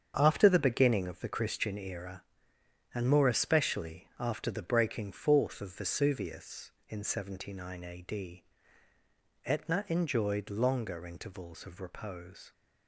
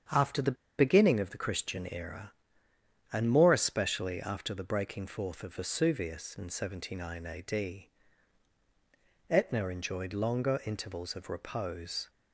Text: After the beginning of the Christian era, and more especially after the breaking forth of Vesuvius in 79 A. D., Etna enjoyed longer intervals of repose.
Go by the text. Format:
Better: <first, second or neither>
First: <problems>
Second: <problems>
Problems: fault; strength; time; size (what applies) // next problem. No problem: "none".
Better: first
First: starts louder than the rest; strong; until 1.1 s; 7.5 dB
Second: starts louder than the rest; strong; until 1.3 s; 7.5 dB // pauses between "the" and "beginning"; slight; at 0.5 s; 0.24 s long